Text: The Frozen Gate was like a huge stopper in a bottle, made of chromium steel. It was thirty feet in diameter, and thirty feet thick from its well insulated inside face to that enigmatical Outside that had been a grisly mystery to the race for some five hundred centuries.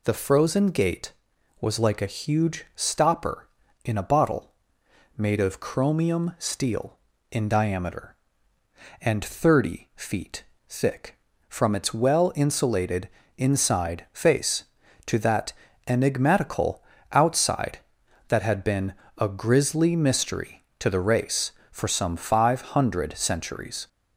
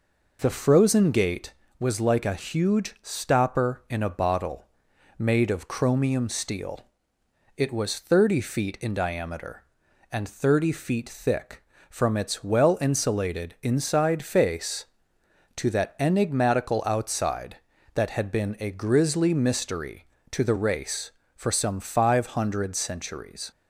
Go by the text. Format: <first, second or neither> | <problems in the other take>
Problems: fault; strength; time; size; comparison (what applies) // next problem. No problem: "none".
second | skips "It was thirty feet"; at 7.1 s // pauses between "feet" and "thick"; slight; at 10.4 s; 0.24 s long // pauses between "insulated" and "inside"; slight; at 13.0 s; 0.28 s long // pauses between "that" and "enigmatical"; slight; at 15.5 s; 0.36 s long // pauses between "enigmatical" and "Outside"; slight; at 16.8 s; 0.28 s long // pauses between "been" and "a"; slight; at 18.9 s; 0.24 s long